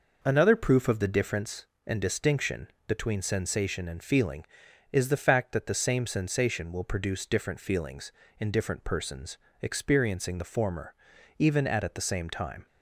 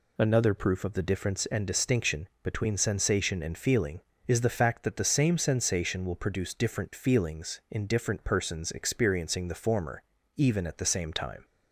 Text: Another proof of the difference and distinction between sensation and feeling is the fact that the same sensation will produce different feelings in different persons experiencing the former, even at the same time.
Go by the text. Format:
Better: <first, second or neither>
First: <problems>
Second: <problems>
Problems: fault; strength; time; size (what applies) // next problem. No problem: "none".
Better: second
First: pauses between "distinction" and "between"; slight; at 2.6 s; 0.20 s long // pauses between "persons" and "experiencing"; slight; at 9.3 s; 0.24 s long // says "at" twice; at 11.8 s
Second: none